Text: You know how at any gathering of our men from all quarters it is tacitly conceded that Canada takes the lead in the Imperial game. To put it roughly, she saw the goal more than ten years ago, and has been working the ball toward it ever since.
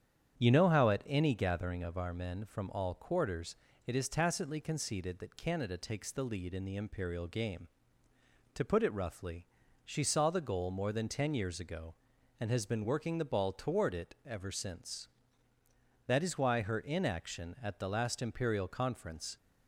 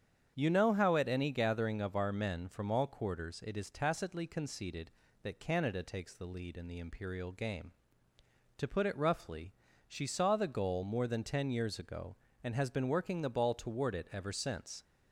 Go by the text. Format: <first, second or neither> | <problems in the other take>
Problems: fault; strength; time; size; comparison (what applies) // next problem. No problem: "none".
second | starts louder than the rest; strong; until 1.4 s; 8.5 dB; strong in the second // pauses between "quarters" and "it"; slight; at 3.5 s; 0.32 s long // goes on to say "That is why her inaction at the last Imperial Conference"; strong; from 16.0 s on; 3.3 s long